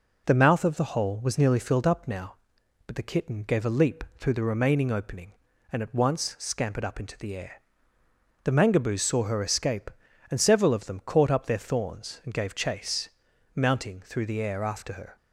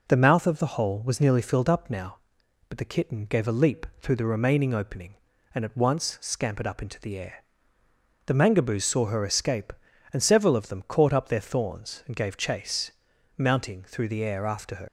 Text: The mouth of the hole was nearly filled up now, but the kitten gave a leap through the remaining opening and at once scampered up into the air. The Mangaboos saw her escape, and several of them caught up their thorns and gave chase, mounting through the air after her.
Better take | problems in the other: first | leaves "her" unfinished; at 14.8 s; 105 ms

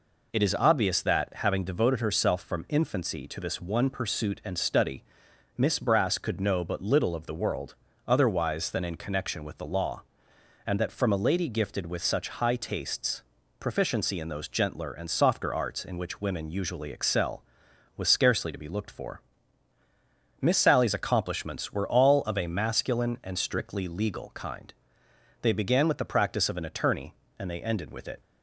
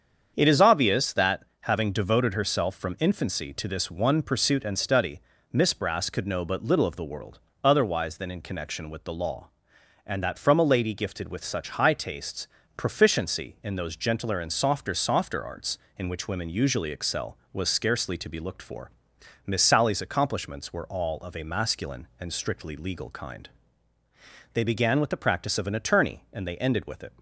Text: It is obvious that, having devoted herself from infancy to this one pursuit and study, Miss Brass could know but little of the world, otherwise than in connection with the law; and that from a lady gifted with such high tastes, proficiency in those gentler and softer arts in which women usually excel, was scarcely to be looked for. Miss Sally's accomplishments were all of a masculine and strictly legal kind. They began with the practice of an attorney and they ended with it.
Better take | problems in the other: first | starts louder than the rest; strong; until 1.3 s; 7.5 dB // says "softer" twice; at 14.9 s

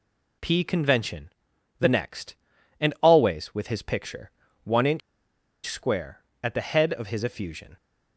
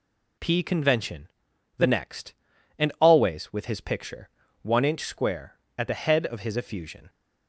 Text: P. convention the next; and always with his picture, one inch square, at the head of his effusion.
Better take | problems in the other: second | pauses between "convention" and "the"; noticeable; at 1.2 s; 0.50 s long; noticeable in the second // pauses between "inch" and "square"; noticeable; at 5.0 s; 0.65 s long

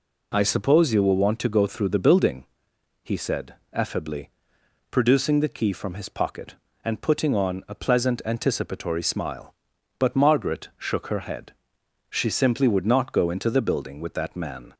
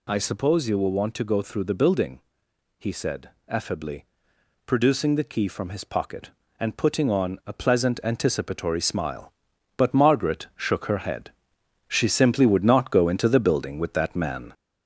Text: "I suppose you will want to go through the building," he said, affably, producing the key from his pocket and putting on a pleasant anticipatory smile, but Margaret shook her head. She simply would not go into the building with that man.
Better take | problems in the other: first | gets louder; noticeable; throughout; 4 dB

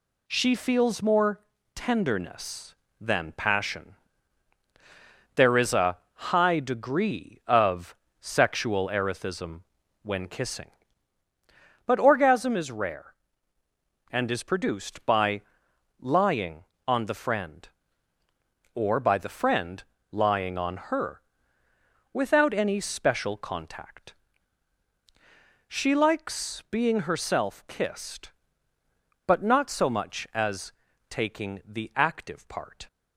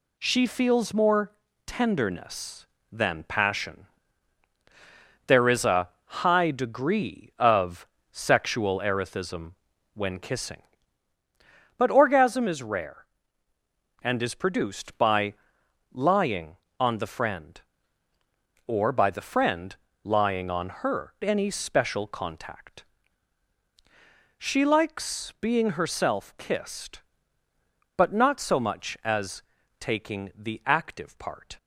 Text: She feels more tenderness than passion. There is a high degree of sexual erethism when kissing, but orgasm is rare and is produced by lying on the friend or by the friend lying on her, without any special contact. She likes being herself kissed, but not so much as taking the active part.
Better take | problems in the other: first | pauses between "more" and "tenderness"; slight; at 1.3 s; 0.34 s long; slight in the first // pauses between "a" and "high"; slight; at 5.8 s; 0.16 s long; slight in the first // pauses between "of" and "sexual"; slight; at 7.8 s; 0.26 s long; slight in the first // pauses between "erethism" and "when"; at 9.5 s; 0.42 s long; also in the first // pauses between "by" and "lying"; noticeable; at 15.3 s; 0.60 s long; noticeable in the first // pauses between "friend" and "lying"; slight; at 19.7 s; 0.28 s long; slight in the first // skips "without"; at 21.1 s // pauses between "as" and "taking"; at 29.4 s; 0.38 s long; also in the first

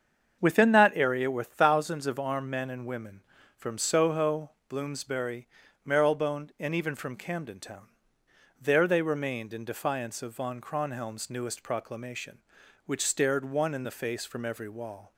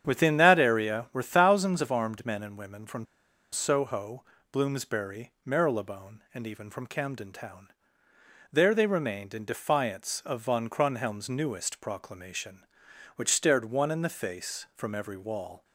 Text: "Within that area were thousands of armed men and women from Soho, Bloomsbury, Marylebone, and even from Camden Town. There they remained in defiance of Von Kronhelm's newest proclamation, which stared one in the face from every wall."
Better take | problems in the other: first | starts louder than the rest; strong; until 1.0 s; 8.5 dB; also in the first // pauses between "from" and "Soho"; noticeable; at 3.0 s; 0.46 s long

